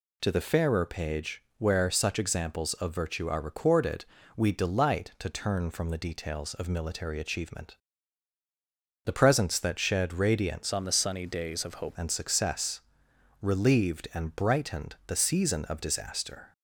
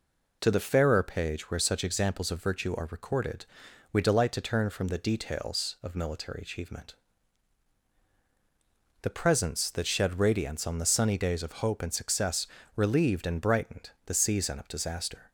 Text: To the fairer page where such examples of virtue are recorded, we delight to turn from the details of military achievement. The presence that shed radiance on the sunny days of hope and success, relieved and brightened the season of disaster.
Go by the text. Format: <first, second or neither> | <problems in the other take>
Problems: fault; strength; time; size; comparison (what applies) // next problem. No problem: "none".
second | pauses between "page" and "where"; slight; at 1.4 s; 0.16 s long // changes voice from "on" to "hope"; from 10.7 to 11.9 s; 1.2 s long